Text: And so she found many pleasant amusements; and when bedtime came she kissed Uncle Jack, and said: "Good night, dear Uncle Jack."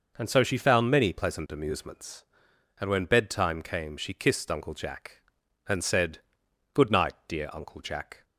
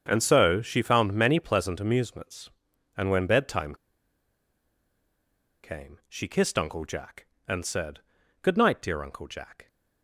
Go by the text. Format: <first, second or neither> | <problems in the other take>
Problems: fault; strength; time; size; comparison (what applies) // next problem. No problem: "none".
first | starts louder than the rest; strong; until 1.0 s; 7.5 dB // pauses between "bedtime" and "came"; strong; at 3.7 s; 1.8 s long